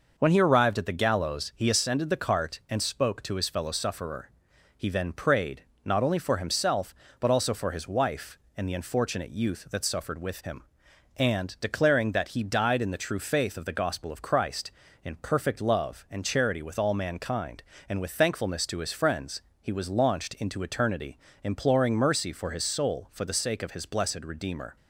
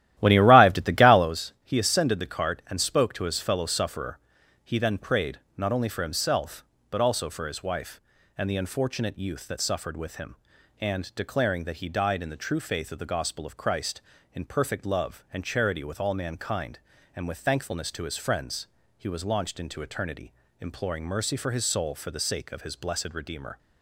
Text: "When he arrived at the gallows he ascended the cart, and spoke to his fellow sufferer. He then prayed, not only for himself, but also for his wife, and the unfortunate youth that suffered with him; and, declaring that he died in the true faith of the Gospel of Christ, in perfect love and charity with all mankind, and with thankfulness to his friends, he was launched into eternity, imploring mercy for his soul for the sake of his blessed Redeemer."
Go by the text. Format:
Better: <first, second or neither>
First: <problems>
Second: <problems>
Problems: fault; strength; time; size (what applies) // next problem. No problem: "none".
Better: first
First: none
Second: starts louder than the rest; strong; until 1.4 s; 13.5 dB